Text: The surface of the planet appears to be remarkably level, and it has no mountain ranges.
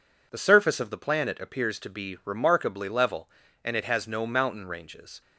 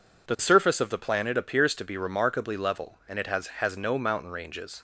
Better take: first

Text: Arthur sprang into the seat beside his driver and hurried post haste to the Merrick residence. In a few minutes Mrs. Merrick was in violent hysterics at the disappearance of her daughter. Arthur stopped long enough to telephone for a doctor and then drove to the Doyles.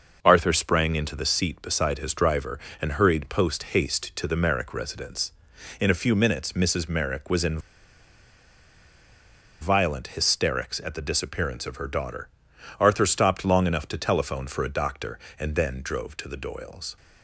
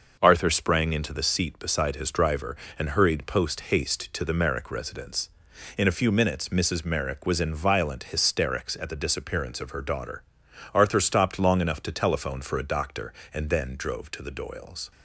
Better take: second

